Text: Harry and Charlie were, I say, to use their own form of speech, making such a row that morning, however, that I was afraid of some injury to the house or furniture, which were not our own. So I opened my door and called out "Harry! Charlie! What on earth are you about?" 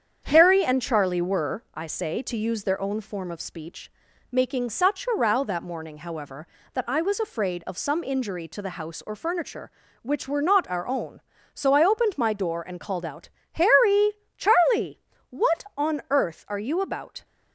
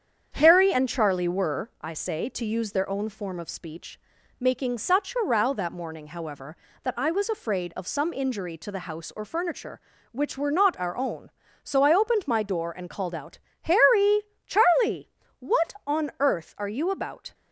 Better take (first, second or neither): neither